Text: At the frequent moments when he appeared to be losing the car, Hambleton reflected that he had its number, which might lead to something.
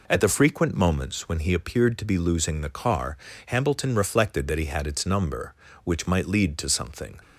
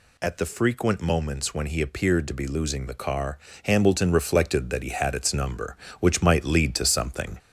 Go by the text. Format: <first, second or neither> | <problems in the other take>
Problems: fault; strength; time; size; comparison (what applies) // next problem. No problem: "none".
first | gets louder; slight; throughout; 2.5 dB